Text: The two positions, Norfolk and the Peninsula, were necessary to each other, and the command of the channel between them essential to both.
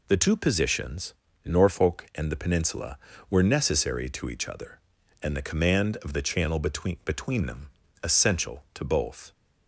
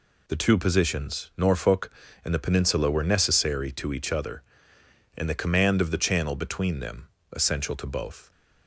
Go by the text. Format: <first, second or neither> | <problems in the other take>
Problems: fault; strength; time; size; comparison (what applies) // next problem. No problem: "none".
second | says "between" twice; at 7.0 s // pauses between "them" and "essential"; slight; at 7.7 s; 0.34 s long; slight in the second